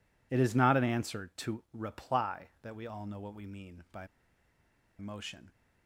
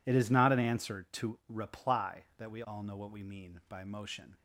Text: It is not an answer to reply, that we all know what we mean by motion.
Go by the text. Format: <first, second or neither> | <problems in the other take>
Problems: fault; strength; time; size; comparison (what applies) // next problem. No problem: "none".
second | pauses between "by" and "motion"; noticeable; at 4.0 s; 0.91 s long